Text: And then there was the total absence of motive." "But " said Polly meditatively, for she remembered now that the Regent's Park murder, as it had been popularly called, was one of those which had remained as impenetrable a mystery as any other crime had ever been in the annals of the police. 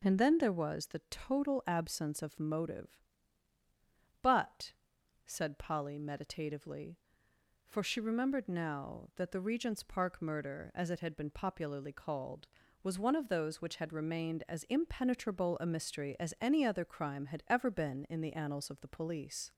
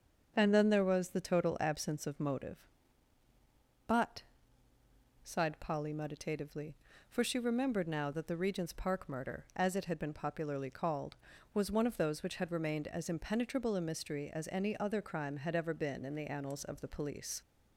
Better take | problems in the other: first | starts louder than the rest; until 1.3 s; 7 dB // says "sighed" for "said"; at 5.2 s

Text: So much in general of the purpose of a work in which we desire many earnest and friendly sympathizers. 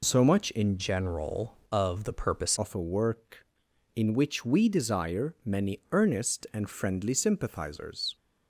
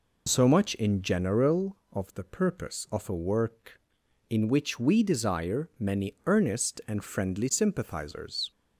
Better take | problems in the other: second | changes voice from "general" to "purpose"; from 0.7 to 2.5 s; 1.8 s long

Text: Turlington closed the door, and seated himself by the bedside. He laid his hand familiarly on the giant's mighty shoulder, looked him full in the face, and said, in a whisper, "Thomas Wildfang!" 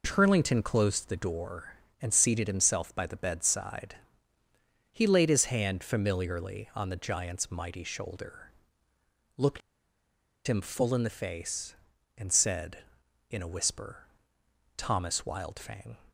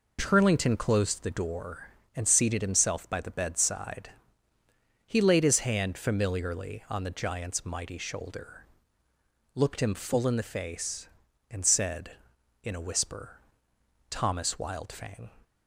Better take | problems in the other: second | pauses between "looked" and "him"; noticeable; at 9.6 s; 0.87 s long

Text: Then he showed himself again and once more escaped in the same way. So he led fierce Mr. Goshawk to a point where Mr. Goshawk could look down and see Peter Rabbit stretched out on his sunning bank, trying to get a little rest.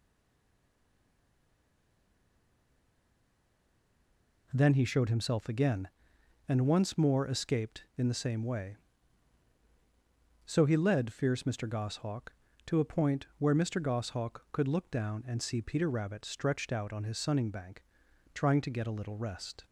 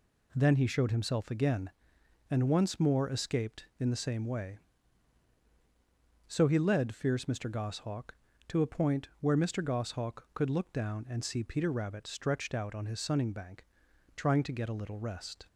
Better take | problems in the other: second | stays silent before the first word; strong; until 4.4 s; 4.4 s long

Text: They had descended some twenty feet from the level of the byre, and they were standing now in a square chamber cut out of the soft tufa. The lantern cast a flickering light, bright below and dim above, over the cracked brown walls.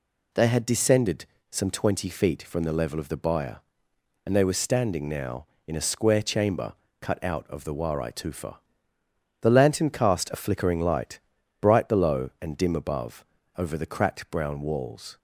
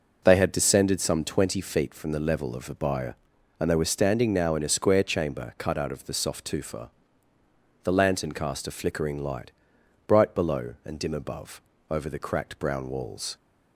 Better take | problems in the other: second | pauses between "descended" and "some"; slight; at 1.2 s; 0.24 s long // pauses between "chamber" and "cut"; slight; at 6.7 s; 0.28 s long // says "warai" for "soft"; at 7.7 s

